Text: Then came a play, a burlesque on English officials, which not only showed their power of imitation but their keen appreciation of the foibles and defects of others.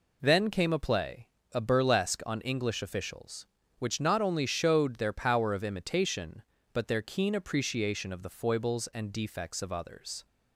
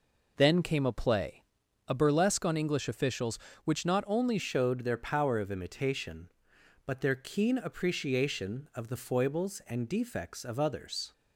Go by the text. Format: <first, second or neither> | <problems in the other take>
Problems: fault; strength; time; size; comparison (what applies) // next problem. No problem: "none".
first | changes voice at "showed"; from 4.3 s on; 6.8 s long